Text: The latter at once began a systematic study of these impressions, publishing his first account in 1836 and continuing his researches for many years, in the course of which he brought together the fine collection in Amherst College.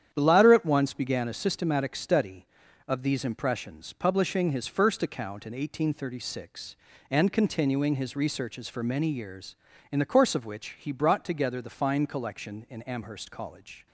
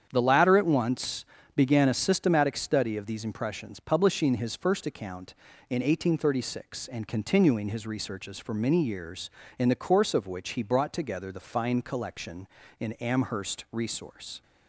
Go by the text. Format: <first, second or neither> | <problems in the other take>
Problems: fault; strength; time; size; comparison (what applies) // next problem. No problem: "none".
first | starts louder than the rest; strong; until 1.1 s; 8.5 dB; strong in the first // pauses between "once" and "began"; slight; at 1.2 s; 0.30 s long // says "Resource" for "College"; at 13.7 s